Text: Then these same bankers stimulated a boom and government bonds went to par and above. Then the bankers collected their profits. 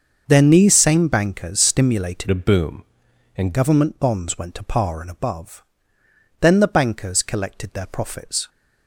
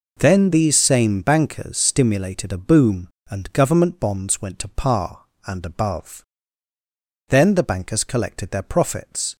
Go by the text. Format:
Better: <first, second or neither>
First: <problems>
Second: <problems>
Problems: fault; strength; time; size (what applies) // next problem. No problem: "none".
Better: second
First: starts louder than the rest; until 1.2 s; 6.5 dB // changes voice from "a" to "and"; from 2.3 to 3.5 s; 1.2 s long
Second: none